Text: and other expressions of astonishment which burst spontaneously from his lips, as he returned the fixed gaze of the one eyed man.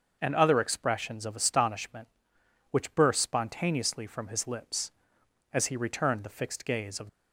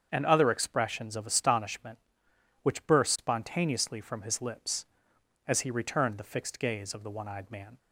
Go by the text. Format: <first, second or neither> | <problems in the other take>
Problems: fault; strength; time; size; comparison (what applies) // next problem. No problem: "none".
second | starts louder than the rest; until 1.2 s; 6 dB; strong in the second // stops before "the one eyed man"; at 7.0 s